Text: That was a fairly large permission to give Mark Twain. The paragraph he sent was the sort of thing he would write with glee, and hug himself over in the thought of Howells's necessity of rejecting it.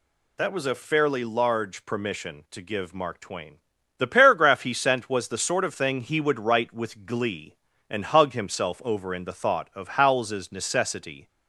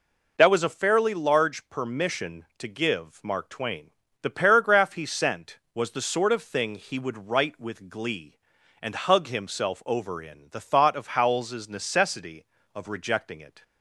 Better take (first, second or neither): second